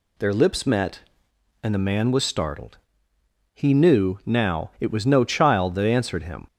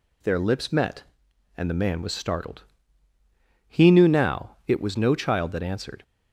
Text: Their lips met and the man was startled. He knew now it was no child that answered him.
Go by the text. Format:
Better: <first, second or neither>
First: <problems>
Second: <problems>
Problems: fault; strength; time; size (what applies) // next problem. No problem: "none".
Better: first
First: none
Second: stops before "him"; at 6.0 s